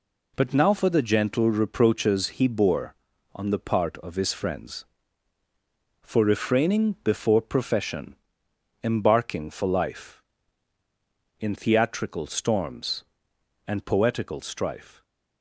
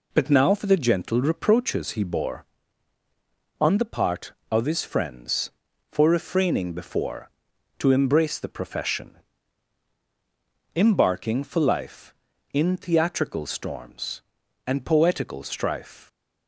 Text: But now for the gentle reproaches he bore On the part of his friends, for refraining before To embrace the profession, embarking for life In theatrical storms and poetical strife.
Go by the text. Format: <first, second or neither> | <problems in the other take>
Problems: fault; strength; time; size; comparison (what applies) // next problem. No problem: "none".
second | skips "To embrace the"; at 7.4 s